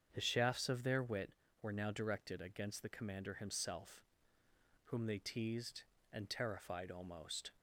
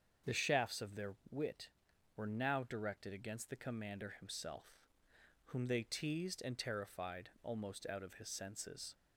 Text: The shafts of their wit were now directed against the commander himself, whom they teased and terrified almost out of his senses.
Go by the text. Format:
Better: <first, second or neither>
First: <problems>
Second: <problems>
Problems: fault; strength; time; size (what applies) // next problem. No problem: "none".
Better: second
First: starts louder than the rest; strong; until 1.1 s; 7.5 dB // stops before "out of his senses"; at 7.5 s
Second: starts louder than the rest; until 1.4 s; 7 dB